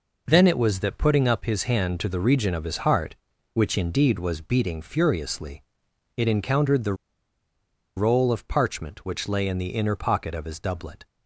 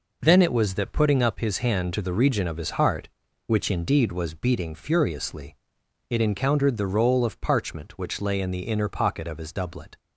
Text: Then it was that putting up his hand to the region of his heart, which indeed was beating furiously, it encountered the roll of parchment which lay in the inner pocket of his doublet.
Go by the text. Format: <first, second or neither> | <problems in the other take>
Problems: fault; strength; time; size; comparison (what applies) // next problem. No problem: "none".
second | pauses between "the" and "roll"; at 6.9 s; 1.0 s long